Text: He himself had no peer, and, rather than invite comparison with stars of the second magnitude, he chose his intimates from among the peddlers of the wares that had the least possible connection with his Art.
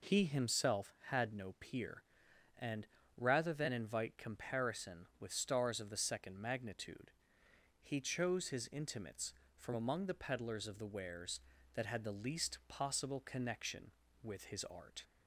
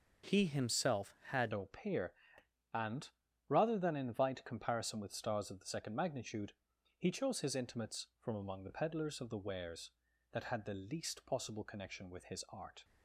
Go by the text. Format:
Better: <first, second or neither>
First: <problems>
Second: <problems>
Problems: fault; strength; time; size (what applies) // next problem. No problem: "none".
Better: first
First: none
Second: starts louder than the rest; noticeable; until 1.4 s; 6 dB // changes voice at "no"; from 1.5 s on; 11.3 s long